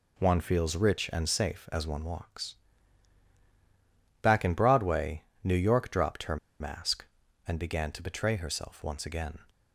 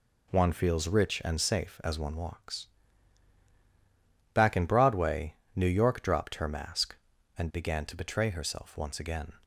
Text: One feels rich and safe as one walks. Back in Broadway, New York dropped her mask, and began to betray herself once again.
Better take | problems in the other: second | pauses between "her" and "mask"; slight; at 6.3 s; 0.23 s long

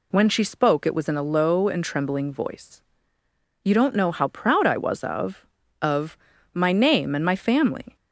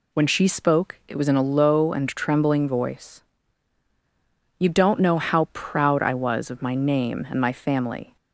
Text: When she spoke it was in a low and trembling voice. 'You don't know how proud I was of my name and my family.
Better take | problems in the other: second | says "of" twice; at 5.8 s

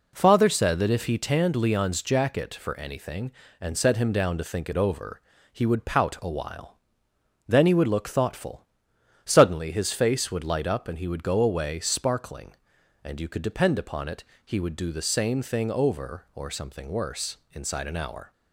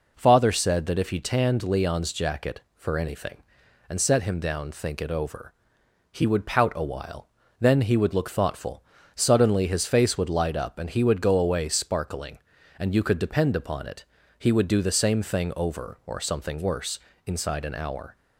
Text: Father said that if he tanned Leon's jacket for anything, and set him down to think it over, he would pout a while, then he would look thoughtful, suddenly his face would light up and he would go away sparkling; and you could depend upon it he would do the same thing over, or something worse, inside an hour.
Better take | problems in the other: first | skips "to"; at 4.7 s // pauses between "it" and "he"; slight; at 14.0 s; 0.34 s long; slight in the first

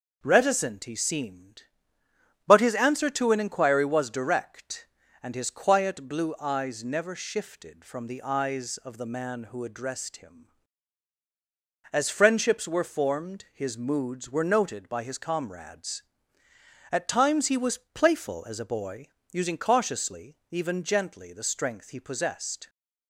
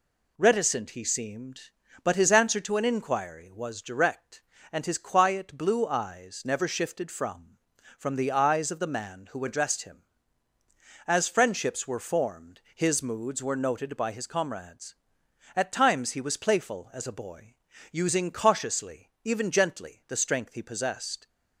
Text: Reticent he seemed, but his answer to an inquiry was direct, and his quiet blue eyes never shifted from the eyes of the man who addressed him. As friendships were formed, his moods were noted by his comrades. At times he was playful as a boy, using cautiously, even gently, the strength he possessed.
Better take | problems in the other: first | says "from" twice; at 7.9 s

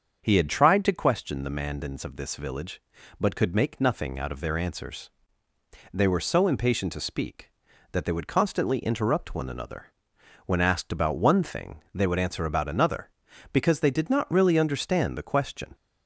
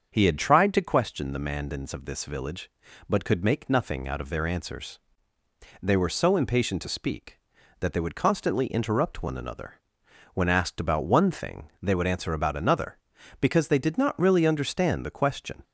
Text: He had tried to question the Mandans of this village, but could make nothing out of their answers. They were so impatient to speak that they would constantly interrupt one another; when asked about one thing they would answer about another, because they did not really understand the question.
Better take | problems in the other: neither | starts louder than the rest; the same in both

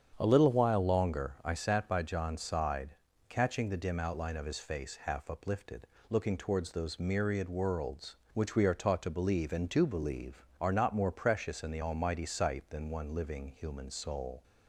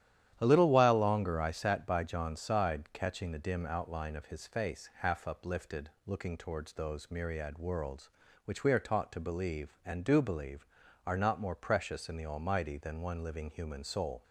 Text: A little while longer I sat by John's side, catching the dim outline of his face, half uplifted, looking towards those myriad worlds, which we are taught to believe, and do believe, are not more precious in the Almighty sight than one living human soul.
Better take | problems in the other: first | starts louder than the rest; strong; until 1.4 s; 11 dB; strong in the first // skips "sight"; at 12.7 s

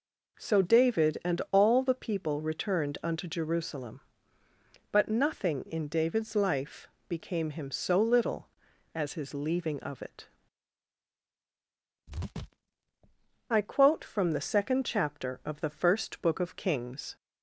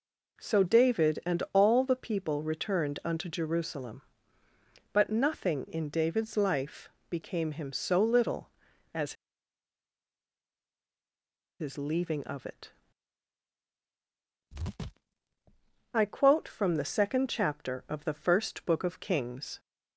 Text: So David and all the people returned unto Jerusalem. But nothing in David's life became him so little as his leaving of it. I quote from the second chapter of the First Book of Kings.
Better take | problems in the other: first | pauses between "life" and "became"; slight; at 6.8 s; 0.20 s long; slight in the first // pauses between "as" and "his"; strong; at 9.1 s; 2.4 s long

